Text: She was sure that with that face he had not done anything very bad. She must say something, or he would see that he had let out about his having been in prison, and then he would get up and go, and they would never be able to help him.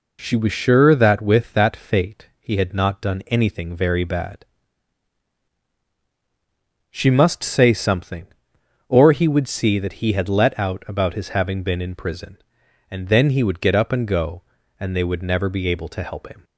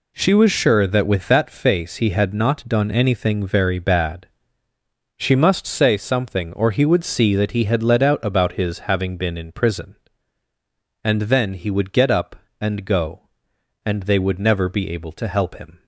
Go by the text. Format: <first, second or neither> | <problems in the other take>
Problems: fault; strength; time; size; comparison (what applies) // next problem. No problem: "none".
second | says "fate" for "face"; at 1.7 s